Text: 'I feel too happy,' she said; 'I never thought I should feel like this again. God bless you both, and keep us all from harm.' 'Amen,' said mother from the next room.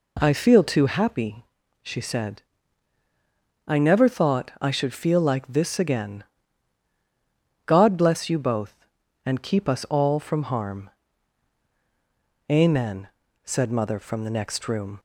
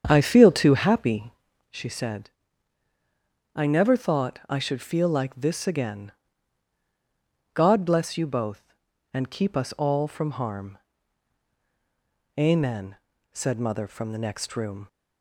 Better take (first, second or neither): first